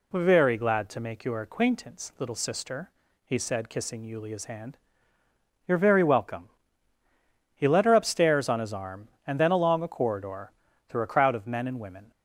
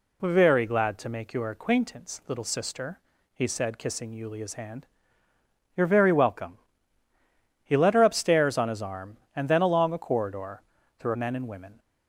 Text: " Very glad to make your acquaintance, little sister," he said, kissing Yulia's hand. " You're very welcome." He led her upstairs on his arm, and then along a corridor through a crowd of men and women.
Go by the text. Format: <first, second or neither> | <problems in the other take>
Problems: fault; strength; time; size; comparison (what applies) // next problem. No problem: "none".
first | pauses between "corridor" and "through"; at 10.6 s; 0.38 s long; also in the first // skips "a crowd of"; at 11.1 s